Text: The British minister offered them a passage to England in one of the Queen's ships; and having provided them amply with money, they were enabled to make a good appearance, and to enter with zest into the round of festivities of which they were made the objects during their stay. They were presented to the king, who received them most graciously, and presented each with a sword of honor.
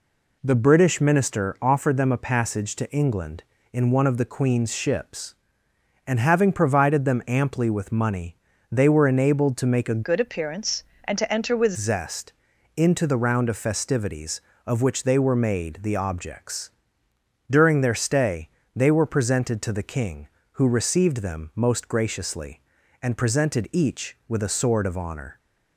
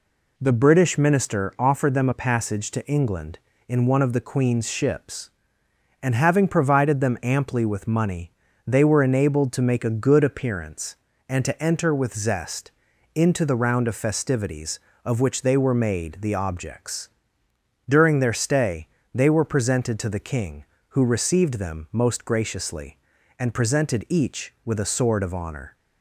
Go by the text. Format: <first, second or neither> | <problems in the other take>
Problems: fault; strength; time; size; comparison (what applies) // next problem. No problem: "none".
second | changes voice from "good" to "with"; from 10.0 to 11.7 s; 1.7 s long // pauses between "zest" and "into"; at 12.3 s; 0.42 s long; also in the second // pauses between "objects" and "during"; noticeable; at 16.6 s; 0.80 s long; noticeable in the second